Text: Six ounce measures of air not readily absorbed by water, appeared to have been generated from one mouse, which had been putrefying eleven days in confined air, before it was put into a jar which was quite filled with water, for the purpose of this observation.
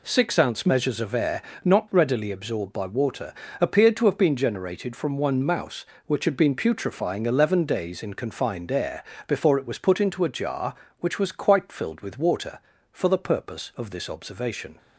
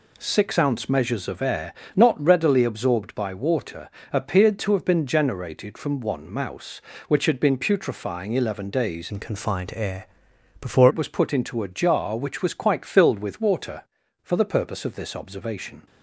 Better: first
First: pauses between "air" and "not"; slight; at 1.4 s; 0.24 s long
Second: pauses between "air" and "not"; slight; at 1.7 s; 0.20 s long // changes voice from "in" to "before"; from 9.1 to 10.8 s; 1.7 s long

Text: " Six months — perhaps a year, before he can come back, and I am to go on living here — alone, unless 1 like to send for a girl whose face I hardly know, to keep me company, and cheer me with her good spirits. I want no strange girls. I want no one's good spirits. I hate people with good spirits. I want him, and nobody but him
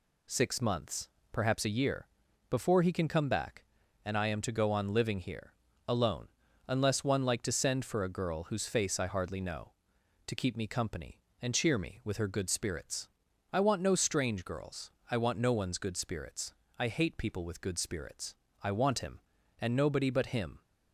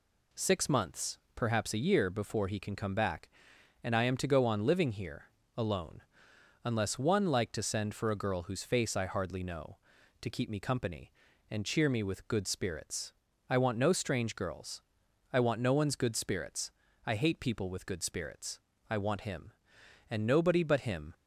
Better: first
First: none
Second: skips "her"; at 12.2 s

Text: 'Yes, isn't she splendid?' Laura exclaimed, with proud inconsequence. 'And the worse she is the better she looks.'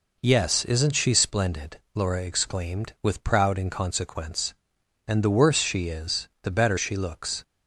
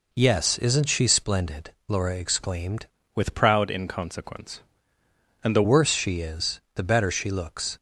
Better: first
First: none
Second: changes voice from "with" to "the"; from 3.1 to 5.6 s; 2.5 s long

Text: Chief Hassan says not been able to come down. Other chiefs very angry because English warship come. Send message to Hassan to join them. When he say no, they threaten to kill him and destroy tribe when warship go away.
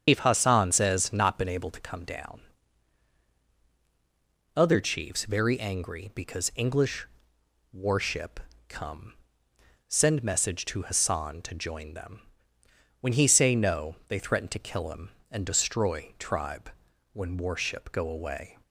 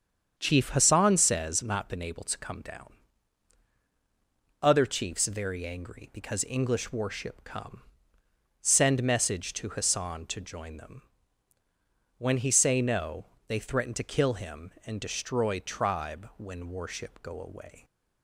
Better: second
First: loses the start of "Chief"; at 0.0 s; 120 ms // starts louder than the rest; strong; until 1.0 s; 8 dB // pauses between "English" and "warship"; noticeable; at 7.0 s; 0.66 s long // pauses between "warship" and "come"; slight; at 8.3 s; 0.30 s long // pauses between "tribe" and "when"; at 16.6 s; 0.44 s long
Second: starts louder than the rest; strong; until 1.3 s; 7.5 dB

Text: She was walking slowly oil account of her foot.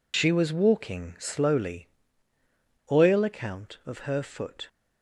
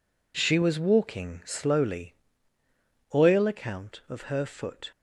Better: second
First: loses the start of "She"; at 0.1 s; 65 ms // pauses between "slowly" and "oil"; at 1.8 s; 1.0 s long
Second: pauses between "slowly" and "oil"; at 2.1 s; 1.0 s long

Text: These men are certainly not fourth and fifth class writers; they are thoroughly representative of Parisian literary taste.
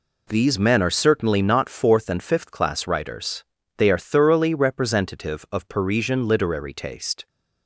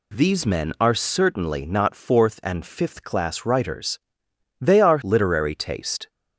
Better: first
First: none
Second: skips "thoroughly representative of Parisian"; at 5.0 s

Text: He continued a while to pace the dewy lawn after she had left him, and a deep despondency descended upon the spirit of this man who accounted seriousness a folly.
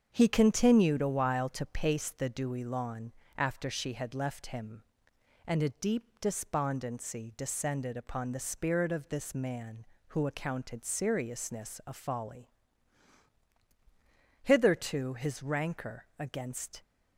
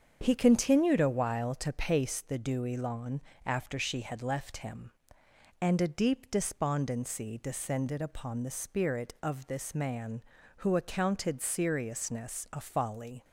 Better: second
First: starts louder than the rest; strong; until 1.1 s; 7.5 dB // pauses between "lawn" and "after"; slight; at 3.1 s; 0.26 s long // goes on to say "Hitherto his rancor against"; strong; from 14.4 s on; 2.4 s long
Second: starts louder than the rest; strong; until 1.2 s; 7.5 dB // pauses between "lawn" and "after"; slight; at 3.1 s; 0.24 s long

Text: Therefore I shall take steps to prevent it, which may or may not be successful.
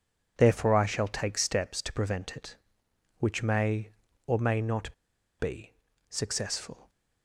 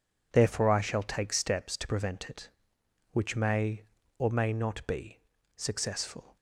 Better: second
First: pauses between "not" and "be"; at 4.9 s; 0.45 s long // pauses between "be" and "successful"; slight; at 5.7 s; 0.36 s long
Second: pauses between "be" and "successful"; slight; at 5.1 s; 0.36 s long

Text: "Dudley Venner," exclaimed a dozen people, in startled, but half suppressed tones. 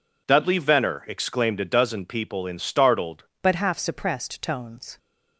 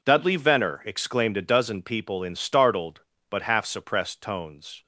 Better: second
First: changes voice at "but"; from 3.4 s on; 1.5 s long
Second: none

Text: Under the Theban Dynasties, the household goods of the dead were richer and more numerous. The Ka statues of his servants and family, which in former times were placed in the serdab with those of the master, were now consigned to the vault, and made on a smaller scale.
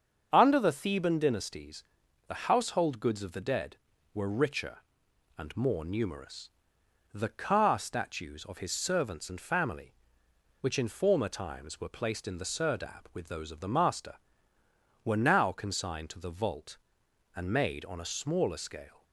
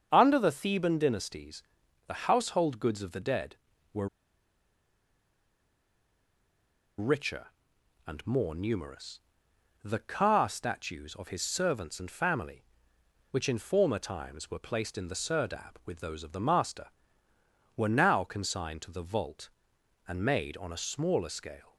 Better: first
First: starts louder than the rest; strong; until 1.3 s; 7 dB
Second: starts louder than the rest; strong; until 1.1 s; 7 dB // pauses between "were" and "richer"; strong; at 4.0 s; 2.9 s long

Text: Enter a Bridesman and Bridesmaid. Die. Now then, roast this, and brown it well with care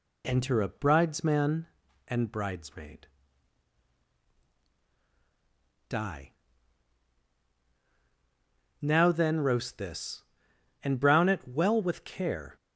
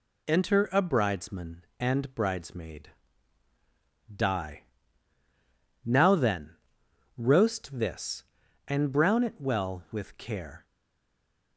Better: first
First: none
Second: stays silent after the last word; slight; from 10.6 s on; 0.9 s long

